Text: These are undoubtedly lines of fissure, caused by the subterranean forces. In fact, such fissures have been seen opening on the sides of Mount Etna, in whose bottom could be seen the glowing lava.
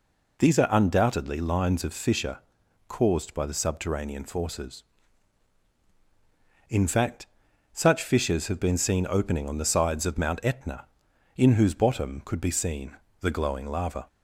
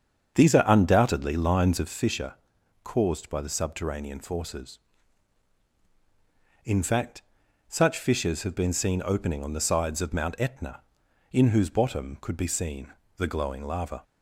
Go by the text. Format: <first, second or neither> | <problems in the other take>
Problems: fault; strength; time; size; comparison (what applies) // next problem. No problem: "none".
first | starts louder than the rest; strong; until 1.9 s; 7.5 dB // pauses between "seen" and "the"; slight; at 12.9 s; 0.24 s long; slight in the first